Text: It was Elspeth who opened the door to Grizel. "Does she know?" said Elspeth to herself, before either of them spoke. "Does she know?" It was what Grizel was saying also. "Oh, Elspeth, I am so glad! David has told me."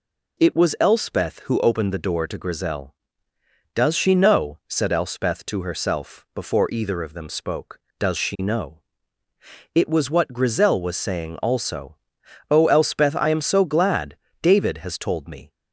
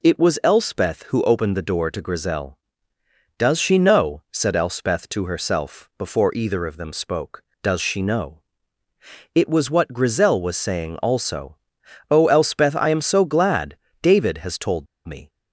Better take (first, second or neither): first